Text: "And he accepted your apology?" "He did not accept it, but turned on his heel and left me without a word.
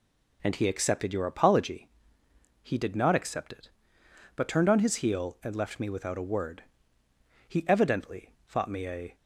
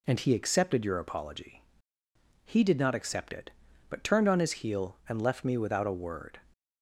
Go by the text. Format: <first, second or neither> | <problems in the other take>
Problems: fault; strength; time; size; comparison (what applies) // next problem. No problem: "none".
second | goes on to say "He evidently thought me a"; strong; from 7.4 s on; 1.6 s long